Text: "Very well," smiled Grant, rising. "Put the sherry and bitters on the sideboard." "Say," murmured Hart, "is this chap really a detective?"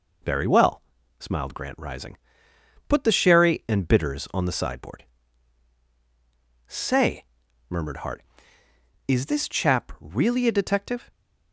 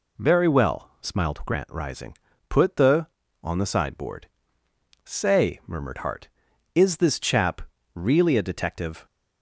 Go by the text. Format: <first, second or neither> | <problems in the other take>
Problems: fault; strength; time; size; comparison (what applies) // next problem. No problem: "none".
first | skips "sherry and bitters"; at 3.2 s // pauses between "chap" and "really"; slight; at 7.5 s; 0.34 s long